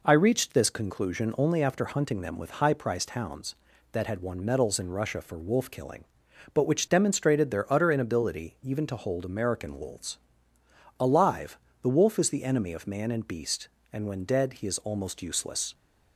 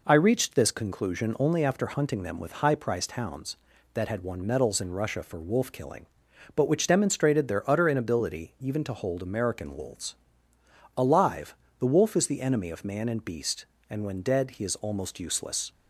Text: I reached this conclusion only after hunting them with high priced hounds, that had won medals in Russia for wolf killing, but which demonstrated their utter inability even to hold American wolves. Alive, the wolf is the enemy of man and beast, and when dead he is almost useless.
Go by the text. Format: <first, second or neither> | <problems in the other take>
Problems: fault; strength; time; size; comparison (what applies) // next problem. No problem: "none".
neither | none